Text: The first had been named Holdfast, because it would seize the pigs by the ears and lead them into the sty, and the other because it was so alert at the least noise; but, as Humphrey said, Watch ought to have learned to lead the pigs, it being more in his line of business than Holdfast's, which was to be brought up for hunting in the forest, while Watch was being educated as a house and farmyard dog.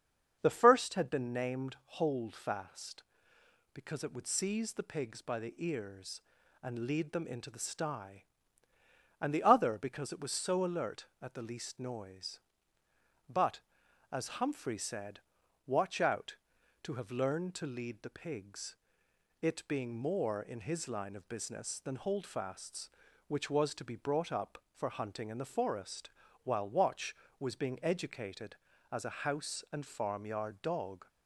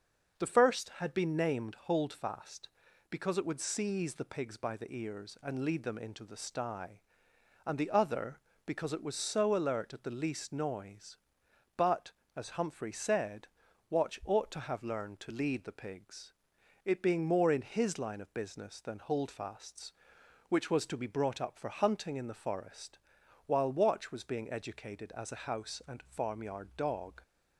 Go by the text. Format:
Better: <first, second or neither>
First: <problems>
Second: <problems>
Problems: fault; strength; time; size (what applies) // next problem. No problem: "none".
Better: second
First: starts louder than the rest; until 1.4 s; 7 dB // pauses between "named" and "Holdfast"; slight; at 1.7 s; 0.22 s long // says "out" for "ought"; at 15.9 s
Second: starts louder than the rest; until 1.4 s; 6.5 dB